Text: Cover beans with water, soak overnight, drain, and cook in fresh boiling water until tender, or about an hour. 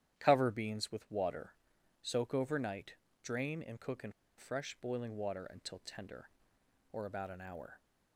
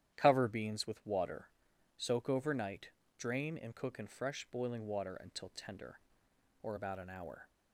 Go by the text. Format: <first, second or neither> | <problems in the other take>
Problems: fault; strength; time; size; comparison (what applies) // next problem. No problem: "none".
second | starts louder than the rest; strong; until 1.2 s; 10.5 dB; strong in the second // pauses between "in" and "fresh"; slight; at 4.1 s; 0.25 s long